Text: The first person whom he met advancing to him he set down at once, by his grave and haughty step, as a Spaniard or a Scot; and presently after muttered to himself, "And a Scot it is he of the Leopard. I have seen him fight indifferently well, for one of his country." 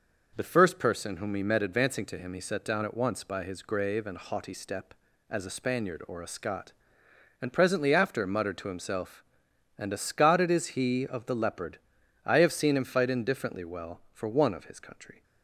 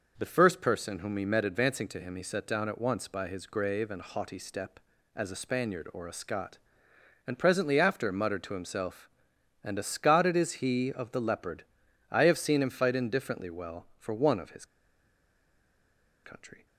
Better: first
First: none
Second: pauses between "his" and "country"; strong; at 14.6 s; 1.5 s long

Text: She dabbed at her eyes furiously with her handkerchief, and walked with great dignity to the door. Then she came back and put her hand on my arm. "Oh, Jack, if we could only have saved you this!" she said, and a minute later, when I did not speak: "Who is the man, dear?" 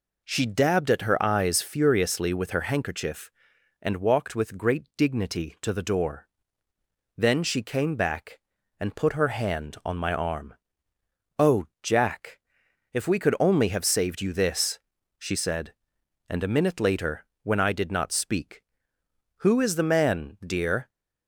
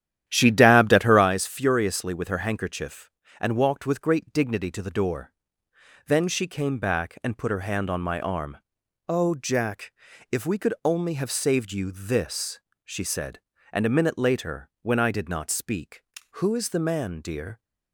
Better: first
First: none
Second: starts louder than the rest; strong; until 1.4 s; 11 dB

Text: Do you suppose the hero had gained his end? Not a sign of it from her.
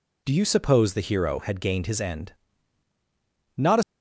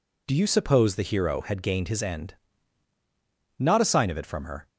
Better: second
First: stops before "sign of it from her"; at 3.8 s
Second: none

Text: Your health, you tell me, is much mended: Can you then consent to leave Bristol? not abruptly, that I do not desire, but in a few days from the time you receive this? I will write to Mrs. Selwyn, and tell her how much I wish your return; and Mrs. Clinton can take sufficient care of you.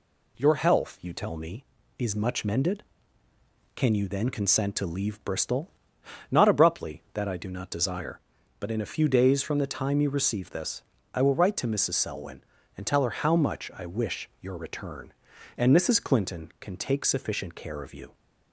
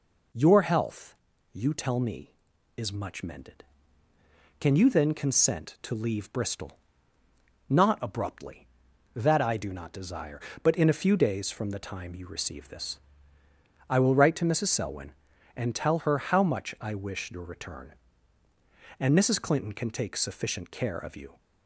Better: neither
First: none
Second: none

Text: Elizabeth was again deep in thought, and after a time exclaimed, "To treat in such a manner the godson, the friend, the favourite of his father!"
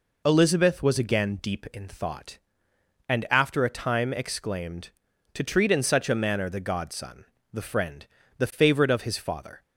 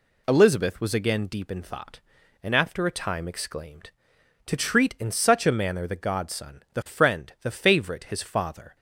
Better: first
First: none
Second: skips "of"; at 8.0 s

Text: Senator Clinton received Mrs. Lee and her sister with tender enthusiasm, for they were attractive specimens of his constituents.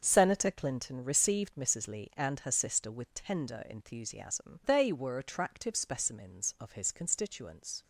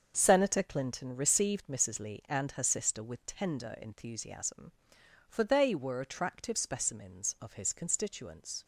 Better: second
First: starts louder than the rest; until 1.0 s; 6.5 dB // skips "for"; at 4.6 s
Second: starts louder than the rest; until 1.1 s; 6.5 dB

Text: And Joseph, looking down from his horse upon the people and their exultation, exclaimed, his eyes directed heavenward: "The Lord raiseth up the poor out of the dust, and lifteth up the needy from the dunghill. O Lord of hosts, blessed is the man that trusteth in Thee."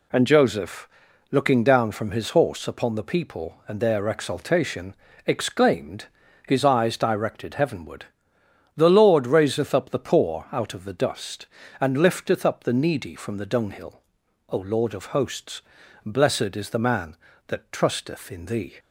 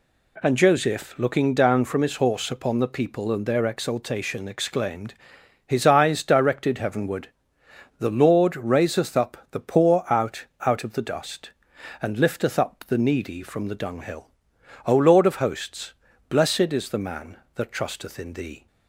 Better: first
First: none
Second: says "out" twice; at 10.6 s

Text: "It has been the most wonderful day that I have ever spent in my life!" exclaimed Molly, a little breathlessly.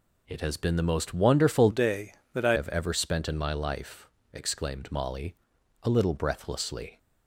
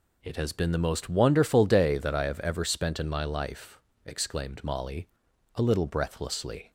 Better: second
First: changes voice from "day" to "I"; from 1.7 to 2.5 s; 0.8 s long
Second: none

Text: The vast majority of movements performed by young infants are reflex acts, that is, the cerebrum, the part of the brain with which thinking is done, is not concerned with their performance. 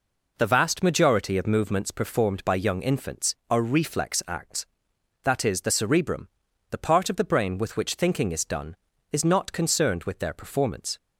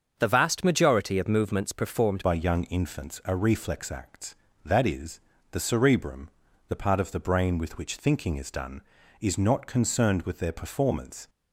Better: first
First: none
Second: starts louder than the rest; until 1.1 s; 6.5 dB // changes voice at "by"; from 2.2 s on; 9.0 s long

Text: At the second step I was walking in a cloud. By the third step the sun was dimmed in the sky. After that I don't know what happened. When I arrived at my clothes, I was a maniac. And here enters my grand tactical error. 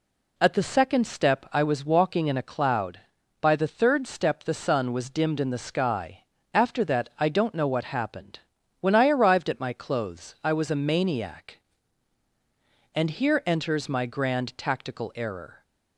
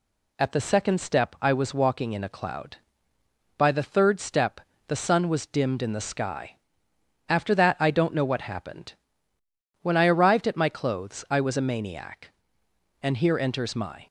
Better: first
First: none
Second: pauses between "step" and "the"; slight; at 4.5 s; 0.30 s long // stops before "grand tactical error"; at 14.0 s

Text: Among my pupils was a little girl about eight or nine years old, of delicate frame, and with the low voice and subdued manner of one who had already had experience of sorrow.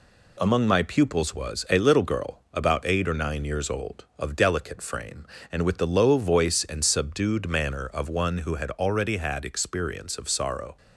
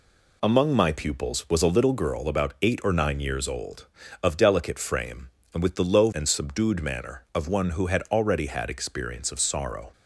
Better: first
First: none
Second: skips "voice"; at 6.1 s

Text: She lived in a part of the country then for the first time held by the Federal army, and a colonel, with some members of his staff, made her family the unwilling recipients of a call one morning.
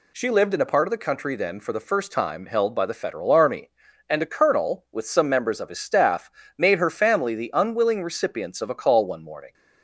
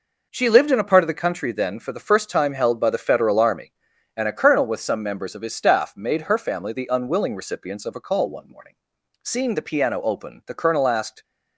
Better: first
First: none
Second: goes on to say "Seeing the piano open the colonel asked"; strong; from 9.2 s on; 2.0 s long

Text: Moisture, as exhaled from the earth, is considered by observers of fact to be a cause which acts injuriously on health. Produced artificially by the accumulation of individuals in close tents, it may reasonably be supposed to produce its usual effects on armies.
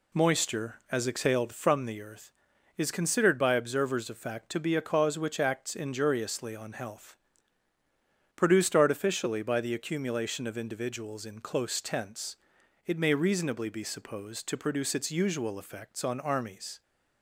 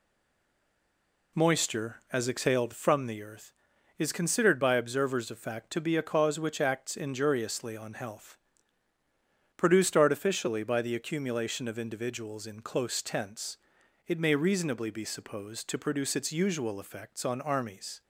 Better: first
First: none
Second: stays silent before the first word; noticeable; until 1.3 s; 1.3 s long

